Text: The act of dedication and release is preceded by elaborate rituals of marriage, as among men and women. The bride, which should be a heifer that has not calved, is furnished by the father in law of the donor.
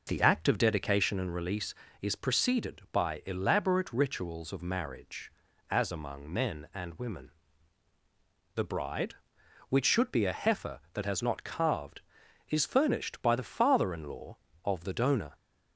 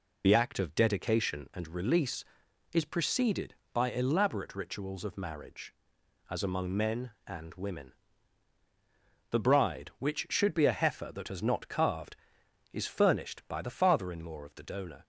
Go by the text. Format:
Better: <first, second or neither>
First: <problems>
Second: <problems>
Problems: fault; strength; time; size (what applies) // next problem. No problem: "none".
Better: first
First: none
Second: loses the start of "The"; at 0.2 s; 30 ms